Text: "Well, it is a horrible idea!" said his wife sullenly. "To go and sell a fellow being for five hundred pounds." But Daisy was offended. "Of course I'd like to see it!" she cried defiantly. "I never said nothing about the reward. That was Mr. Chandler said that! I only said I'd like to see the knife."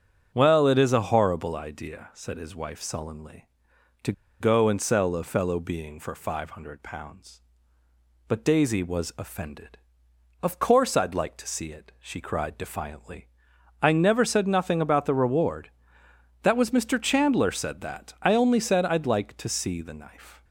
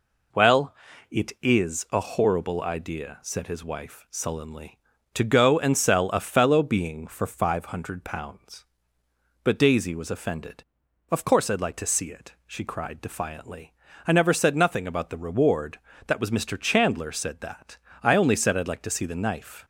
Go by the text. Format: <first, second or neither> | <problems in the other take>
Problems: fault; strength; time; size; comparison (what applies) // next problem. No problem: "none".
second | starts louder than the rest; until 1.3 s; 7 dB // pauses between "To" and "go"; slight; at 4.1 s; 0.27 s long